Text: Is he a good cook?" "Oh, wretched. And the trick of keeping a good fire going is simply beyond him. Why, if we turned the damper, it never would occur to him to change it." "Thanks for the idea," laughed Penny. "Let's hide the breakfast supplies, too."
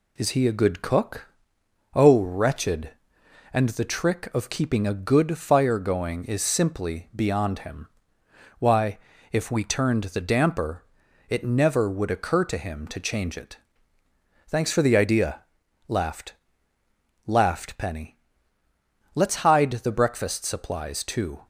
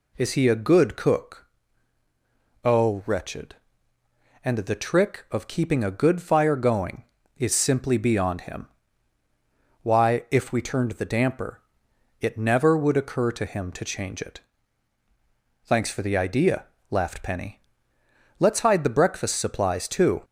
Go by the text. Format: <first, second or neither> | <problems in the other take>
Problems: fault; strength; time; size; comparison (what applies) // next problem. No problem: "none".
second | says "laughed" twice; at 17.2 s